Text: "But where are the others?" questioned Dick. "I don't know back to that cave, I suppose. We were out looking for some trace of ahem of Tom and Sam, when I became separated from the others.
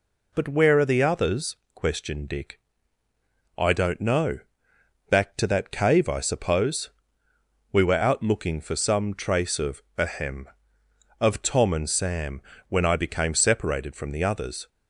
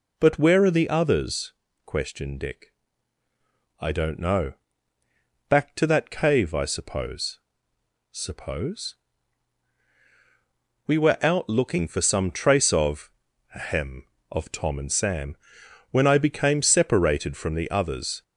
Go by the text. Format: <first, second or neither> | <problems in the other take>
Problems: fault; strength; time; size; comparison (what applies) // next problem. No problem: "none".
first | pauses between "know" and "back"; noticeable; at 4.5 s; 0.96 s long; noticeable in the first // says "suppose" twice; at 8.1 s // pauses between "of" and "ahem"; noticeable; at 13.1 s; 0.46 s long; slight in the first